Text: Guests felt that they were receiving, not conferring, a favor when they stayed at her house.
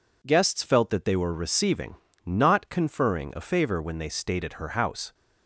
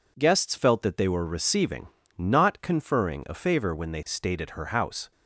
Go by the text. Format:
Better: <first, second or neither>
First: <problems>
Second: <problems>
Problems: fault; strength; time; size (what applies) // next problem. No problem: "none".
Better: neither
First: none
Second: none